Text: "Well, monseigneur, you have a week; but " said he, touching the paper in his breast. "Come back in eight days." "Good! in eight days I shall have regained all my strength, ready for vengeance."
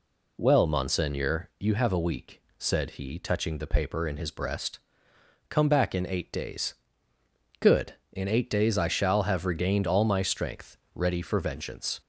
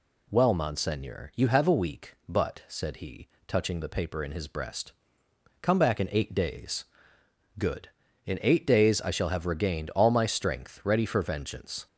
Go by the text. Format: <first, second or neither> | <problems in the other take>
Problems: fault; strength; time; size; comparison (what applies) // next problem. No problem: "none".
second | skips "but"; at 2.4 s